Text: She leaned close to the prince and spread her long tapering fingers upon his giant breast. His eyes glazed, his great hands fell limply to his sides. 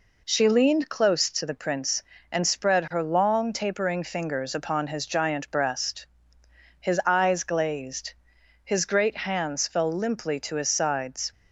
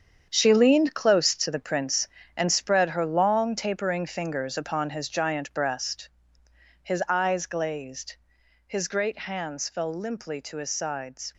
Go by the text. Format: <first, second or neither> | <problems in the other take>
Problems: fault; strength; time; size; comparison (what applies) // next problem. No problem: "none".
first | gets quieter; strong; throughout; 11 dB